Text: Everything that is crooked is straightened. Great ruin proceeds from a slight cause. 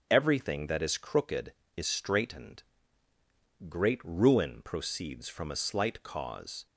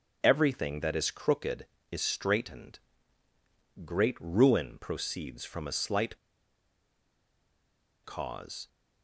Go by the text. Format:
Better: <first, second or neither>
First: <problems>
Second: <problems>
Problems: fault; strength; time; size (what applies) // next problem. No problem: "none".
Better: first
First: starts louder than the rest; strong; until 1.1 s; 7.5 dB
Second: starts louder than the rest; strong; until 1.2 s; 7 dB // pauses between "slight" and "cause"; strong; at 6.1 s; 1.8 s long